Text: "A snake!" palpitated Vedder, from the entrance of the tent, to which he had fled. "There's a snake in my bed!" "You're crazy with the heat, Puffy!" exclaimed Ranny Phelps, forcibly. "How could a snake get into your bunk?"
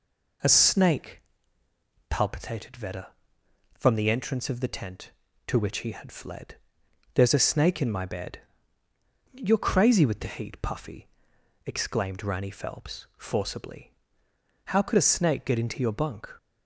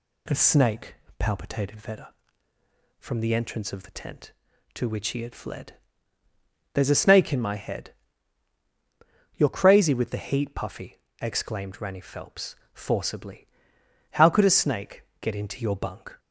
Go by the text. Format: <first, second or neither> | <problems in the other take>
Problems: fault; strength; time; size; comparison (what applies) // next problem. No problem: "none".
first | says "head" for "bed"; at 7.5 s // pauses between "snake" and "get"; slight; at 15.0 s; 0.16 s long